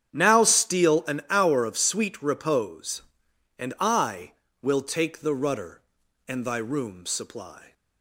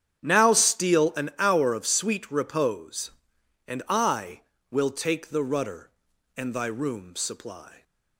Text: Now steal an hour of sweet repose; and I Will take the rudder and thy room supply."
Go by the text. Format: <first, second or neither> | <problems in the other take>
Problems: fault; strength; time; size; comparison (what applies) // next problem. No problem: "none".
neither | starts louder than the rest; strong; the same in both